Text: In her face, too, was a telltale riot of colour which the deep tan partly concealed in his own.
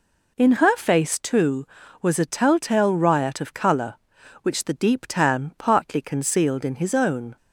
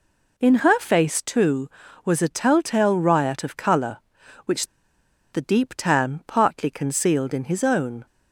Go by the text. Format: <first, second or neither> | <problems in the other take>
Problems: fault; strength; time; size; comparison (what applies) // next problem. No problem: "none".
first | pauses between "which" and "the"; noticeable; at 4.6 s; 0.65 s long